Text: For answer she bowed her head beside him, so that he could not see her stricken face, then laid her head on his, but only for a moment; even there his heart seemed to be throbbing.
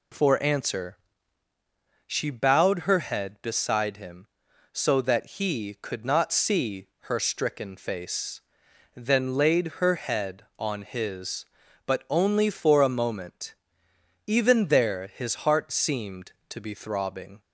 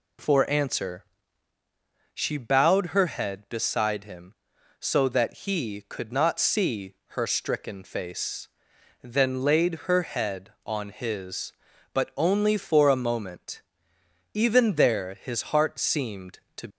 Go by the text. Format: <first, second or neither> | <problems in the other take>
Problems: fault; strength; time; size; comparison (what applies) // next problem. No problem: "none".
first | pauses between "answer" and "she"; at 1.0 s; 1.0 s long; also in the first // pauses between "see" and "her"; slight; at 6.9 s; 0.22 s long; slight in the first // stops before "be throbbing"; at 16.6 s